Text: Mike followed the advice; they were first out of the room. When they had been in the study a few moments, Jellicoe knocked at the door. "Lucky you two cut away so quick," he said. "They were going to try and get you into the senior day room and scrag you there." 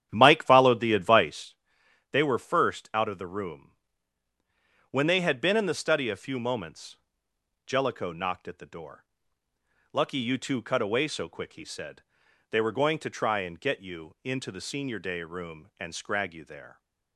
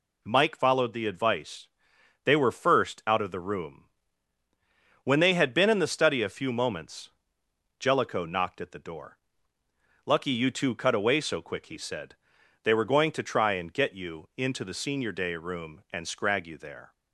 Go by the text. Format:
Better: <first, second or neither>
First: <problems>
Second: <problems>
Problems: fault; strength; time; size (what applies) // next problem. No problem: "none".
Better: second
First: starts louder than the rest; strong; until 1.6 s; 10 dB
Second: none